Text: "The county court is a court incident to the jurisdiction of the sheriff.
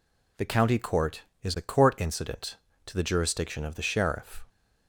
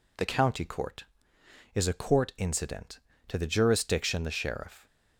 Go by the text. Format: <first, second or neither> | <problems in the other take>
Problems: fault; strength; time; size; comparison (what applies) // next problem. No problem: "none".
first | skips "of"; at 4.2 s